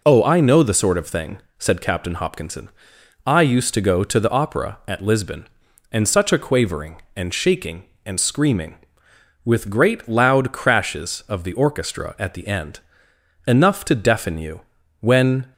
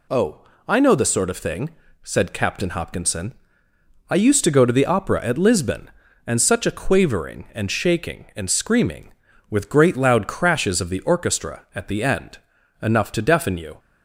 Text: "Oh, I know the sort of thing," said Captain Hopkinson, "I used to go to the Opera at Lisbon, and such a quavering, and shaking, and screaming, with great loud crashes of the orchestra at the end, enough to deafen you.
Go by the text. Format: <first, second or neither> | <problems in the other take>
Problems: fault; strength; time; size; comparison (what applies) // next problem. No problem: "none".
second | goes on to say "When"; from 14.9 s on; 0.54 s long